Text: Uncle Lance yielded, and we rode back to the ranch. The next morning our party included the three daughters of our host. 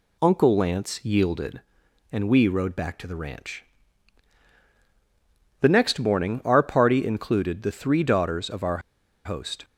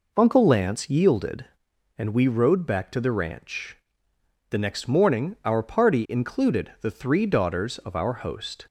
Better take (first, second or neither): second